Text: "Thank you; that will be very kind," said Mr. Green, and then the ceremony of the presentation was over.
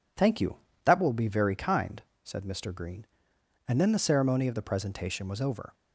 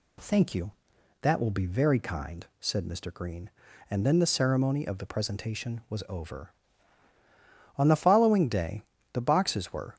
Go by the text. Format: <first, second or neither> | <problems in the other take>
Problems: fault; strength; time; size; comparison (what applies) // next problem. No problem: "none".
first | goes on to say "On the following day the boxes were"; strong; from 7.7 s on; 2.1 s long